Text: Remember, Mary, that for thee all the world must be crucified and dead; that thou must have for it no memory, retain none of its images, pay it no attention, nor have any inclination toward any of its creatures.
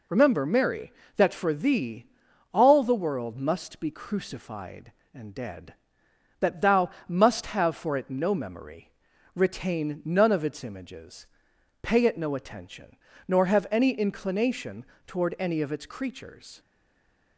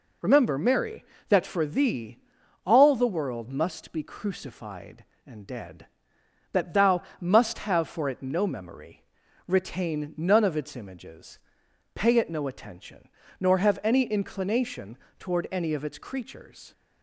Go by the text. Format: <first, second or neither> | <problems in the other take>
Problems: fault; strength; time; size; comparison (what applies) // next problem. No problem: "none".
second | pauses between "thee" and "all"; noticeable; at 2.0 s; 0.46 s long; noticeable in the second // pauses between "thou" and "must"; slight; at 6.8 s; 0.18 s long; slight in the second // pauses between "inclination" and "toward"; slight; at 14.8 s; 0.22 s long; slight in the second // stays silent after the last word; slight; from 16.5 s on; 0.8 s long